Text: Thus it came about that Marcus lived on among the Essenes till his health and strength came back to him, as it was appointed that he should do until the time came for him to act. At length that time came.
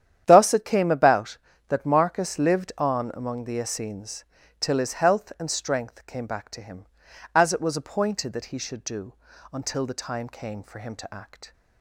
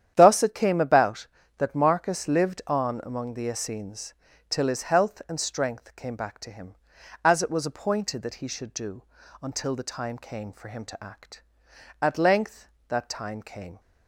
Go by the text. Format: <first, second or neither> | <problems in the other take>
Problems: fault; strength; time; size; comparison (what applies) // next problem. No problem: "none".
second | starts louder than the rest; strong; until 1.2 s; 10 dB; strong in the second // pauses between "Essenes" and "till"; slight; at 4.2 s; 0.34 s long; slight in the second // pauses between "do" and "until"; at 9.1 s; 0.38 s long; also in the second // stops before "At length that time came"; at 11.5 s